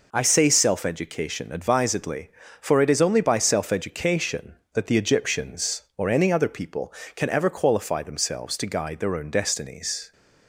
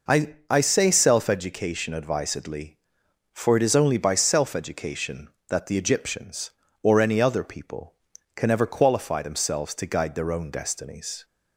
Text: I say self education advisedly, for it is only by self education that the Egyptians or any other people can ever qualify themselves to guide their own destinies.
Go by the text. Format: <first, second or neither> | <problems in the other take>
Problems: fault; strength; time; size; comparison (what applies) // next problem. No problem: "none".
first | says "I" twice; at 0.4 s